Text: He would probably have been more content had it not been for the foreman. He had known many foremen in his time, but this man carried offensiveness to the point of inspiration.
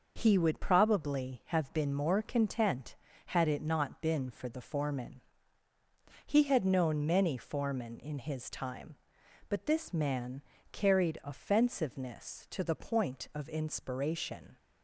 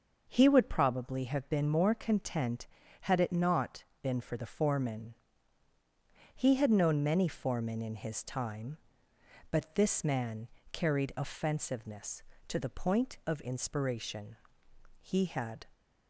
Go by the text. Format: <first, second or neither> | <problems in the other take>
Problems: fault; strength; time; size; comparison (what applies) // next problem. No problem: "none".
first | pauses between "not" and "been"; slight; at 3.8 s; 0.18 s long // pauses between "man" and "carried"; slight; at 10.4 s; 0.24 s long; slight in the first // goes on to say "He had"; noticeable; from 15.0 s on; 0.68 s long